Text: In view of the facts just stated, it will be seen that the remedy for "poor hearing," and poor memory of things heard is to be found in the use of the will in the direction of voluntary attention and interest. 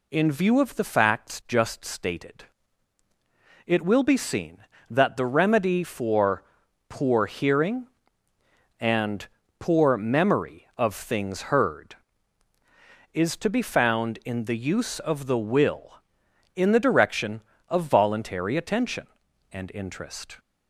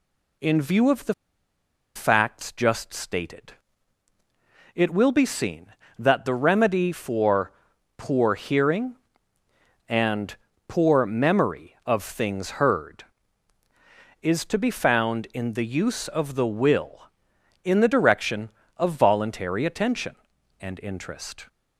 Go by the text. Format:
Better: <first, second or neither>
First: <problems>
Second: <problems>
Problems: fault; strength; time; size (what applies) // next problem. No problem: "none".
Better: first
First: pauses between "for" and "poor"; noticeable; at 6.4 s; 0.46 s long // pauses between "and" and "poor"; slight; at 9.2 s; 0.32 s long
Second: pauses between "the" and "facts"; noticeable; at 1.1 s; 0.81 s long // pauses between "for" and "poor"; noticeable; at 7.5 s; 0.46 s long // pauses between "and" and "poor"; slight; at 10.3 s; 0.32 s long